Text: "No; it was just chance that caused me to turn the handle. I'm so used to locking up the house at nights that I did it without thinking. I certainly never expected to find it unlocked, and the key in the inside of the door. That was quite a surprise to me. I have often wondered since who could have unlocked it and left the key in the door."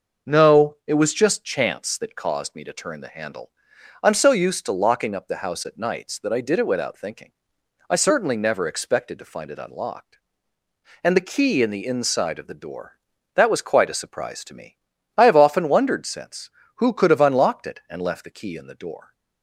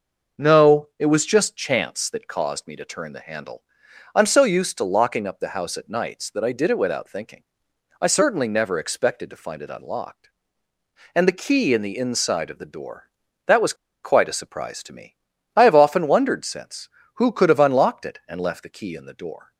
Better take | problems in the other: first | pauses between "was" and "quite"; slight; at 13.7 s; 0.29 s long

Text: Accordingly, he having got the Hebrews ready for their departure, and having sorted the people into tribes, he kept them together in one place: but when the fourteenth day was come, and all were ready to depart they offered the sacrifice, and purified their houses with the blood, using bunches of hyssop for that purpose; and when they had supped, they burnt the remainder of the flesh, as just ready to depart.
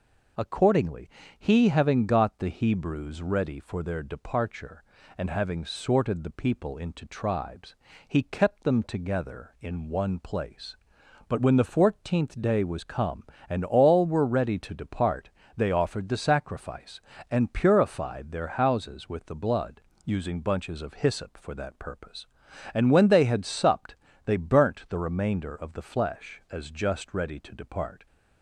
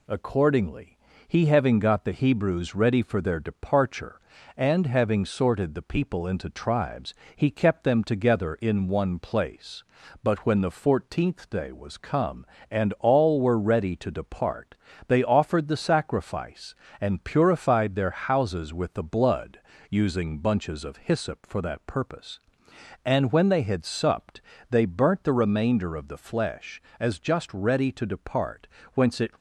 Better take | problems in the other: first | pauses between "depart" and "they"; slight; at 14.7 s; 0.32 s long; slight in the first // goes on to say "Whence it"; slight; from 28.9 s on; 0.36 s long

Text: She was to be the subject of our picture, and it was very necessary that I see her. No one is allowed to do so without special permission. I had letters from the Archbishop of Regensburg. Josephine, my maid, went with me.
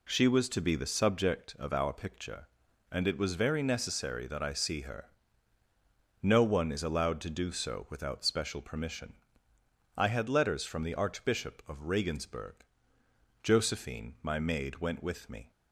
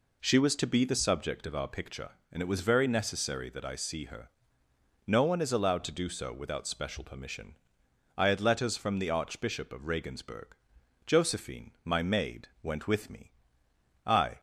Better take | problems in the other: first | goes on to say "I"; slight; from 14.0 s on; 0.34 s long

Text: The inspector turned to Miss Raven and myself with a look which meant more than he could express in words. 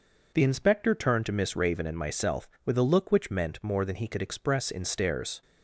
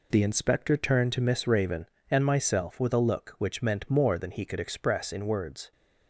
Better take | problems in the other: second | says "stares" for "words"; at 4.8 s

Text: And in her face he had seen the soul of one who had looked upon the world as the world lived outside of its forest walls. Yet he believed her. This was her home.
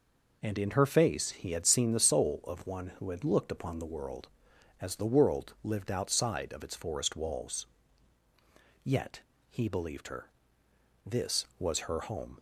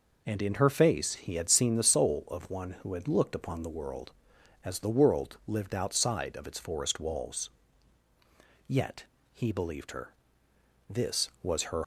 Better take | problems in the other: first | pauses between "Yet" and "he"; slight; at 9.0 s; 0.28 s long; slight in the first // stops before "home"; at 11.8 s

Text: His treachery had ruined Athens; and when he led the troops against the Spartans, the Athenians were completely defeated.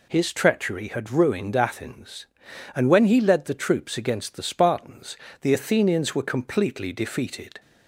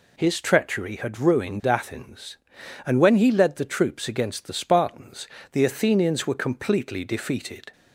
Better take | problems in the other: neither | none

